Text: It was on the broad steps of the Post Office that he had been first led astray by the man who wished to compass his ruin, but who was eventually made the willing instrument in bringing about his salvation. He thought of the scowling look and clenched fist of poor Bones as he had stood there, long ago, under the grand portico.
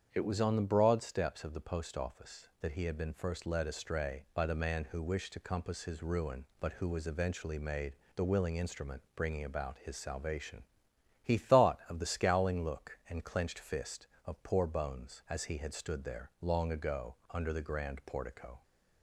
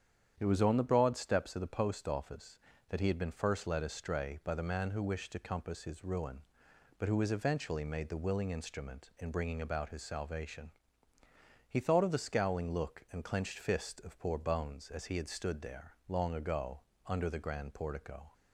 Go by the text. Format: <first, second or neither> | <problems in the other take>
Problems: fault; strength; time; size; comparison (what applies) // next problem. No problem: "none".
second | starts louder than the rest; strong; until 1.1 s; 7.5 dB; strong in the second // pauses between "made" and "the"; slight; at 7.9 s; 0.24 s long // skips "in"; at 9.0 s